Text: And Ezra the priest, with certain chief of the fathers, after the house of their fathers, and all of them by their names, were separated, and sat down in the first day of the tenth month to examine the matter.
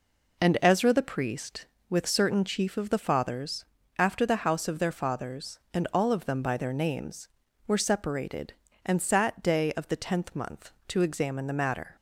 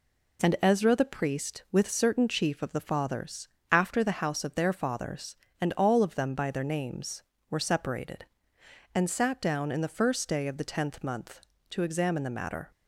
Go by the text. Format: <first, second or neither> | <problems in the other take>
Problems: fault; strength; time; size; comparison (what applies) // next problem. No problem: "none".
second | skips "down in the first"; at 9.4 s